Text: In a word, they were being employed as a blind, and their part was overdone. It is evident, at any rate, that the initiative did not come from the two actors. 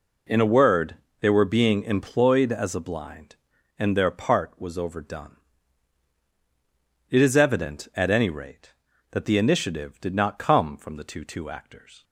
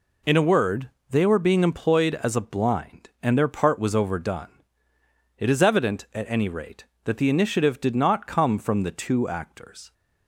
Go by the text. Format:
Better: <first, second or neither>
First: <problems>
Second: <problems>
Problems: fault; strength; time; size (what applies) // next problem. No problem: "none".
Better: second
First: says "two" twice; at 11.2 s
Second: none